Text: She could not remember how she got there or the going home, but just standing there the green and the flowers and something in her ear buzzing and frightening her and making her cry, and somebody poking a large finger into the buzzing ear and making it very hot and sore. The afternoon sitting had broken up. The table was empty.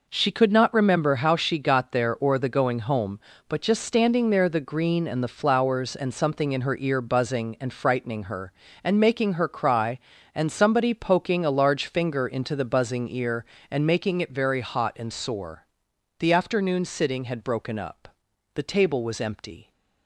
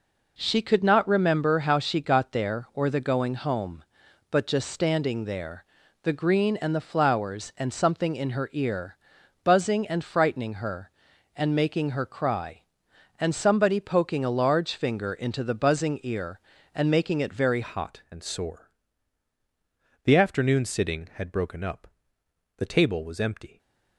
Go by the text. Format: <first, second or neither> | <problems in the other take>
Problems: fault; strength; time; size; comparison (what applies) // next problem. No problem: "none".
first | pauses between "there" and "the"; at 5.6 s; 0.38 s long // pauses between "ear" and "buzzing"; noticeable; at 8.9 s; 0.46 s long // changes voice at "hot"; from 17.6 s on; 5.9 s long